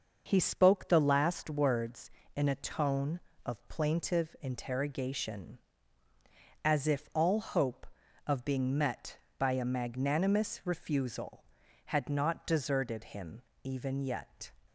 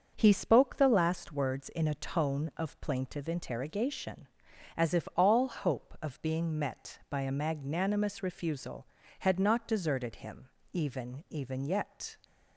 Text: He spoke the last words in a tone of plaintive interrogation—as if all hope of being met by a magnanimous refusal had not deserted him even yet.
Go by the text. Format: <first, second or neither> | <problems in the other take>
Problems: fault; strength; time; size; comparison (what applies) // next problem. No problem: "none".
first | starts louder than the rest; until 1.1 s; 6.5 dB; noticeable in the first // pauses between "him" and "even"; slight; at 10.4 s; 0.24 s long; slight in the first // says "even" twice; at 11.2 s